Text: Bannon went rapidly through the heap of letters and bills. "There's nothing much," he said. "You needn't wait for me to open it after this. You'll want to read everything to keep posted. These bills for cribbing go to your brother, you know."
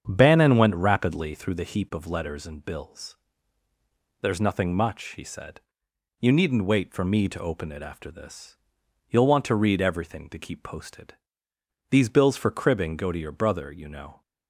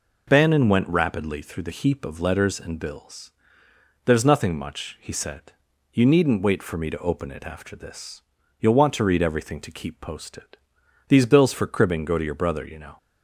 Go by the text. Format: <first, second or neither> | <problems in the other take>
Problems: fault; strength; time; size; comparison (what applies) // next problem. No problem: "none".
second | starts louder than the rest; strong; until 1.6 s; 7.5 dB